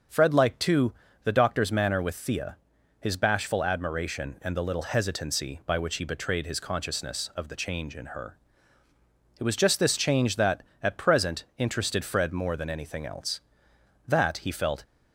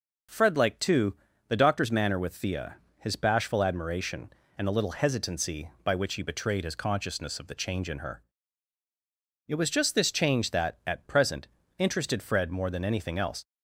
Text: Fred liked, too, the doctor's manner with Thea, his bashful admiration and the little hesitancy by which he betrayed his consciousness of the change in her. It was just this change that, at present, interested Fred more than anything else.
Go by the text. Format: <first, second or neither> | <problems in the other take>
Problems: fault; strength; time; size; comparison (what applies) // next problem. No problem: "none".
second | starts louder than the rest; until 1.4 s; 6.5 dB // goes on to say "That he felt"; noticeable; from 14.0 s on; 0.78 s long